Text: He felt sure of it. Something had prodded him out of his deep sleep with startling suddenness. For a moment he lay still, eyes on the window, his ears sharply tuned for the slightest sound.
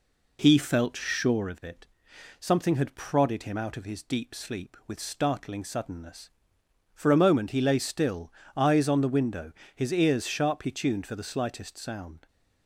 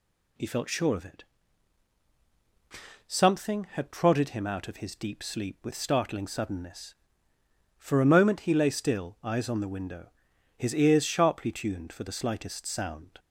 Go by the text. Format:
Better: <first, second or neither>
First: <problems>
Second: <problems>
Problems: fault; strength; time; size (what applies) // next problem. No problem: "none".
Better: second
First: starts louder than the rest; slight; until 1.4 s; 3 dB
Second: none